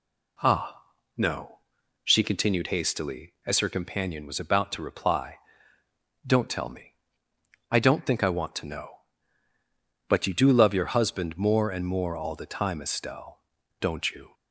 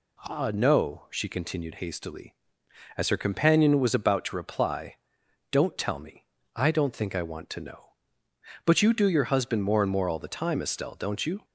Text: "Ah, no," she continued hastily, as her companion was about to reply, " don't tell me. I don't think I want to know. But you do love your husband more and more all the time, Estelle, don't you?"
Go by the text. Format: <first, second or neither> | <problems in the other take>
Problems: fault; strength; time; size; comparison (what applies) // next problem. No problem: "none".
first | skips "love"; at 9.0 s